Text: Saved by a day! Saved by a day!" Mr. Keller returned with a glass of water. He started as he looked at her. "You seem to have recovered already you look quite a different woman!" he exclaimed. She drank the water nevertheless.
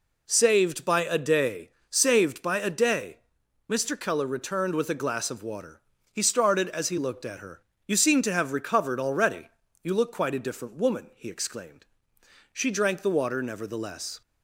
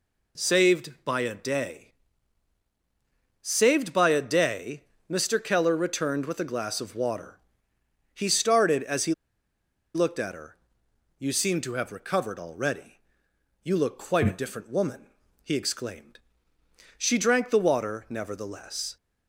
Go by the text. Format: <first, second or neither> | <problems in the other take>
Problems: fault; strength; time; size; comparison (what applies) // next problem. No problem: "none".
first | pauses between "he" and "looked"; noticeable; at 9.1 s; 0.80 s long // pauses between "already" and "you"; noticeable; at 12.9 s; 0.64 s long; slight in the first